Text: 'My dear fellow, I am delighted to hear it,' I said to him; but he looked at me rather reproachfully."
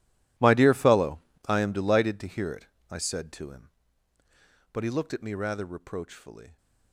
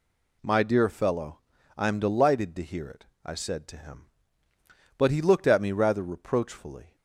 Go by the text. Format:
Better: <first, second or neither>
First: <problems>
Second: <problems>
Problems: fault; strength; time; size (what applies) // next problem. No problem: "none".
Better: second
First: gets quieter; strong; throughout; 19 dB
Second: none